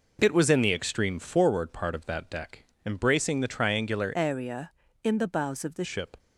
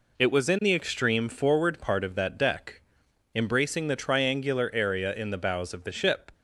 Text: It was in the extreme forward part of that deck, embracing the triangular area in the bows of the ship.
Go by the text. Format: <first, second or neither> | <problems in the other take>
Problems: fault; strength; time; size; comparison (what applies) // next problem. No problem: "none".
second | changes voice from "area" to "the"; from 4.1 to 5.8 s; 1.7 s long